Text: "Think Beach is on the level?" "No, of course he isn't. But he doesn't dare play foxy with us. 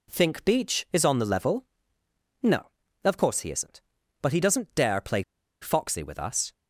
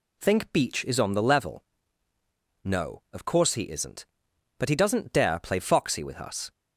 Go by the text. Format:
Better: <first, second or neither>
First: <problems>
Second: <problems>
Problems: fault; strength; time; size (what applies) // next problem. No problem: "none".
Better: second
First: pauses between "play" and "foxy"; at 5.2 s; 0.40 s long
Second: none